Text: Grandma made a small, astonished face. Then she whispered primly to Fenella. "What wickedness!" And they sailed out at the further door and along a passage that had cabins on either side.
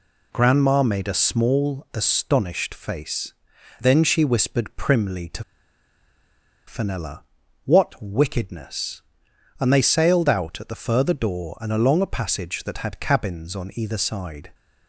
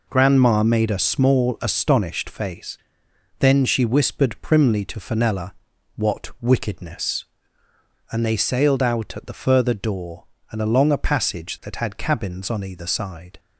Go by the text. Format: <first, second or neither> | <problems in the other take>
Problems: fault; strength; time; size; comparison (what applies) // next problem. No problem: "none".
second | pauses between "to" and "Fenella"; strong; at 5.4 s; 1.2 s long